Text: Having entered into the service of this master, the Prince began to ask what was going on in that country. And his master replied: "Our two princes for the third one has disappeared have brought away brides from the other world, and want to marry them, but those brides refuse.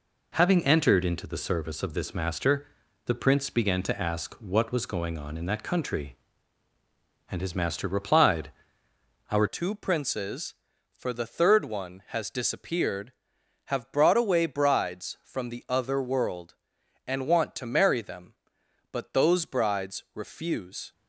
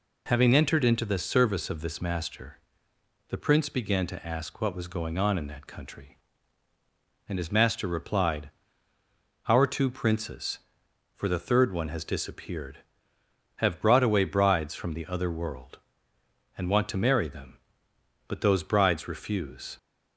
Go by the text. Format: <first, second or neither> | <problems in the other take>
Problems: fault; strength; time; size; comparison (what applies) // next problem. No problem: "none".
second | changes voice at "two"; from 9.4 s on; 11.5 s long